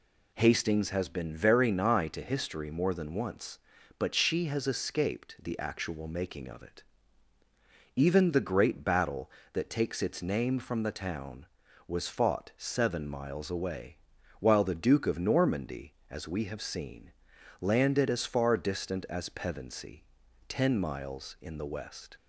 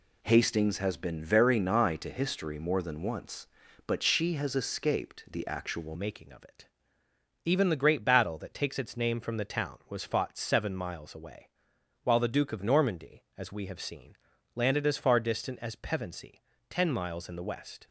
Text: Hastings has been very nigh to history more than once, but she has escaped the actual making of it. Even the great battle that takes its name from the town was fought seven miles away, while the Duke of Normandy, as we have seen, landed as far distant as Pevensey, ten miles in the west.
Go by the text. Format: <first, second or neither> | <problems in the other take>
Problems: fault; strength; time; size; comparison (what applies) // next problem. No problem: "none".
first | changes voice at "making"; from 5.9 s on; 11.9 s long